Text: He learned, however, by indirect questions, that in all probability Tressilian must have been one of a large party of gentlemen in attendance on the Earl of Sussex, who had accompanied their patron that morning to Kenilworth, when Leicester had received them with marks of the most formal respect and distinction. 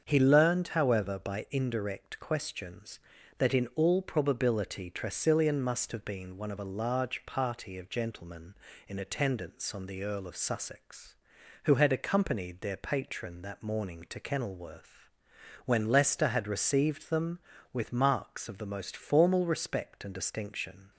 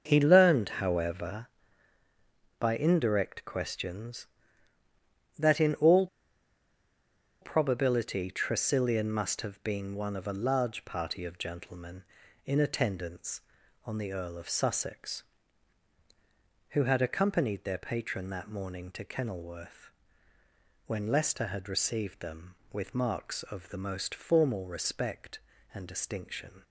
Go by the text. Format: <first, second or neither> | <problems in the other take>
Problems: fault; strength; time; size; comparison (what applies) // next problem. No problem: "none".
first | starts louder than the rest; until 1.0 s; 6.5 dB; also in the first // pauses between "all" and "probability"; strong; at 6.0 s; 1.3 s long